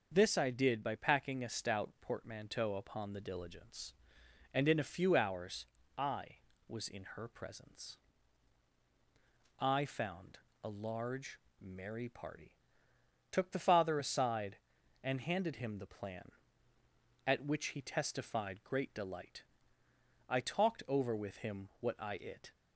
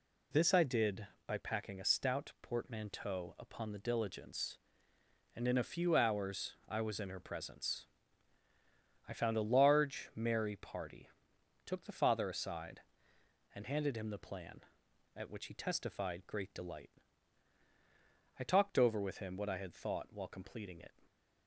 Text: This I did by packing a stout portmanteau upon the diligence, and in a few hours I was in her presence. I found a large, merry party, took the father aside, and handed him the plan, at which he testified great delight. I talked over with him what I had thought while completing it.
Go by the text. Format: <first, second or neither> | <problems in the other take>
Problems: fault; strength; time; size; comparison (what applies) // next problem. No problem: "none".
second | starts louder than the rest; noticeable; until 1.1 s; 6 dB // pauses between "hours" and "I"; slight; at 5.6 s; 0.32 s long // pauses between "found" and "a"; slight; at 10.3 s; 0.26 s long // skips "had thought while completing"; at 22.1 s